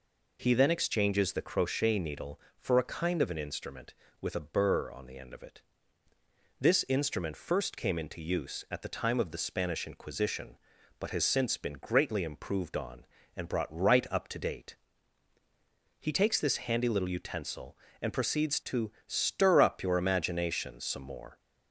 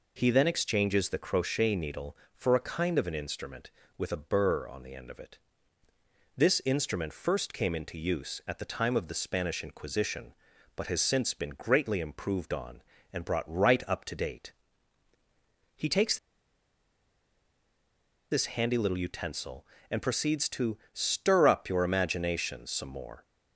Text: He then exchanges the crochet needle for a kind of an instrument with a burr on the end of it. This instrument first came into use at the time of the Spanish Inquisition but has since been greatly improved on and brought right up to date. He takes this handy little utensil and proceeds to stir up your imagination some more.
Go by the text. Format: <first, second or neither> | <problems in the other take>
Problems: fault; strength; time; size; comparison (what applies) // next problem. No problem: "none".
first | pauses between "takes" and "this"; strong; at 16.1 s; 2.1 s long // pauses between "to" and "stir"; slight; at 20.7 s; 0.16 s long; slight in the first